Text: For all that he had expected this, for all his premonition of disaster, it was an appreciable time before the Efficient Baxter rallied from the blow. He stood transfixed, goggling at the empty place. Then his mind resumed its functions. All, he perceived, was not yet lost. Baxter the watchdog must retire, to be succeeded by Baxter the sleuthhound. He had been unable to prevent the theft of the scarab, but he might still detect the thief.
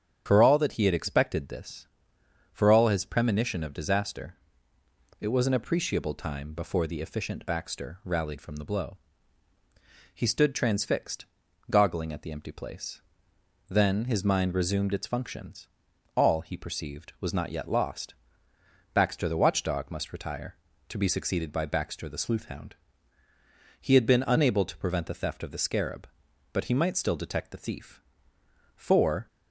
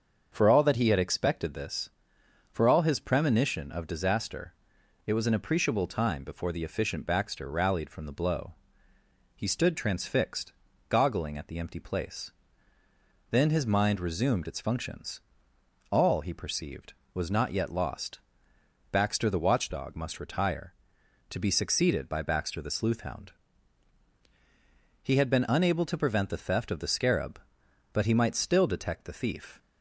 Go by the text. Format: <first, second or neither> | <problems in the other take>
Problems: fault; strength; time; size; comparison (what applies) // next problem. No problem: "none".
second | starts louder than the rest; strong; until 1.2 s; 8 dB; also in the second // goes on to say "For"; from 28.7 s on; 0.52 s long